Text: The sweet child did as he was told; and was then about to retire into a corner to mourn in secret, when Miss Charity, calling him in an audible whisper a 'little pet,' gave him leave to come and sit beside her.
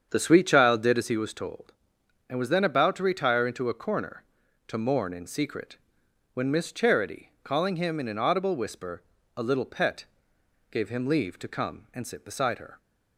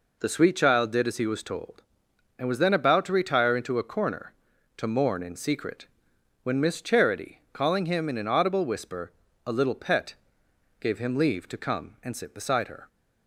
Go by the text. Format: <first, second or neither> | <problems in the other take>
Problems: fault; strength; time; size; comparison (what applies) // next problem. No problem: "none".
second | starts louder than the rest; strong; until 1.3 s; 7.5 dB // pauses between "whisper" and "a"; slight; at 9.0 s; 0.34 s long; slight in the second